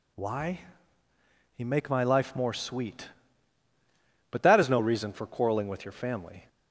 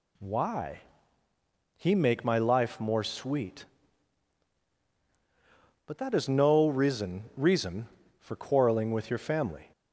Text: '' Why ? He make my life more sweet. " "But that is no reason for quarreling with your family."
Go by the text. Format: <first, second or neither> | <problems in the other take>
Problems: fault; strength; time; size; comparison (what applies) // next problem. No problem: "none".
first | says "reason" twice; at 7.3 s